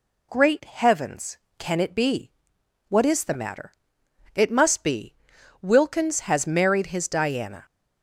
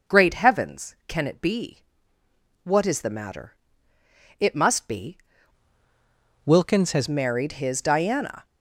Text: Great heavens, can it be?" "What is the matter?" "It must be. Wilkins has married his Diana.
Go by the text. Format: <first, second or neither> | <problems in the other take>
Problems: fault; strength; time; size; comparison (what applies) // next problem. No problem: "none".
first | changes voice from "Wilkins" to "has"; from 6.4 to 7.0 s; 0.6 s long